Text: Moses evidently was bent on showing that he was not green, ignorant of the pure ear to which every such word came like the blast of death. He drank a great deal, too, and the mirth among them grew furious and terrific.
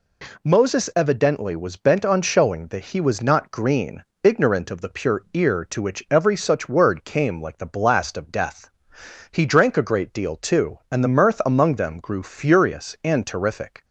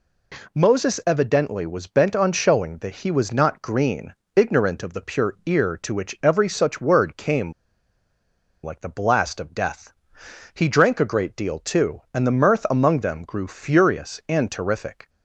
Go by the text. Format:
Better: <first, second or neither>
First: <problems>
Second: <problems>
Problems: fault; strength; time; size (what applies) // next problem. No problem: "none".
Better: first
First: none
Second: pauses between "came" and "like"; at 7.5 s; 1.1 s long